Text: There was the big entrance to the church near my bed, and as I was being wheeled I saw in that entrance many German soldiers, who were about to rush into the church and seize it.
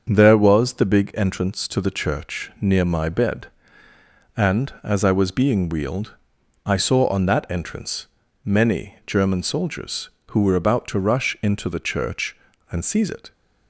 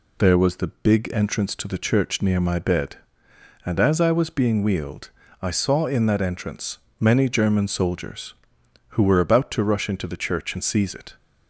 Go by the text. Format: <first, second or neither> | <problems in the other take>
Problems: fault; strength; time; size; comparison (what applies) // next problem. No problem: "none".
second | starts louder than the rest; until 1.1 s; 6.5 dB // pauses between "wheeled" and "I"; noticeable; at 6.1 s; 0.50 s long; slight in the second // says "on" for "in"; at 7.0 s // pauses between "entrance" and "many"; slight; at 8.0 s; 0.36 s long; slight in the second